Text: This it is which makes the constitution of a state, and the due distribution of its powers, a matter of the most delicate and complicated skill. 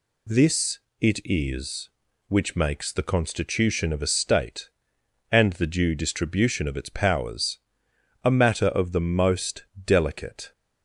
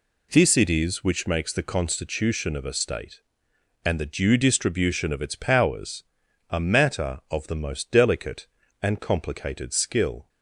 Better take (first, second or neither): second